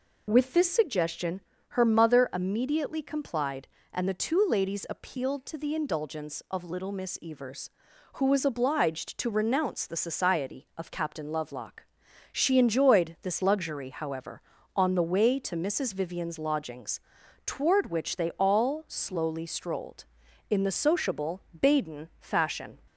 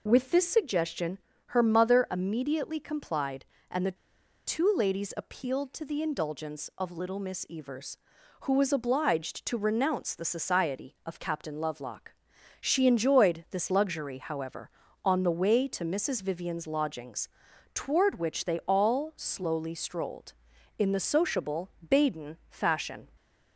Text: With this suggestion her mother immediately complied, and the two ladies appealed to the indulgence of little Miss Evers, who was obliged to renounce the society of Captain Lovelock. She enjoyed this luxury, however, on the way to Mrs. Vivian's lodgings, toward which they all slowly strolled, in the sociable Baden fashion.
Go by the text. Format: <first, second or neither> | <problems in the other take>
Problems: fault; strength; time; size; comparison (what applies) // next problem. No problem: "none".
first | pauses between "suggestion" and "her"; slight; at 1.1 s; 0.28 s long; slight in the first // pauses between "the" and "two"; noticeable; at 3.9 s; 0.51 s long // pauses between "sociable" and "Baden"; slight; at 21.6 s; 0.18 s long; slight in the first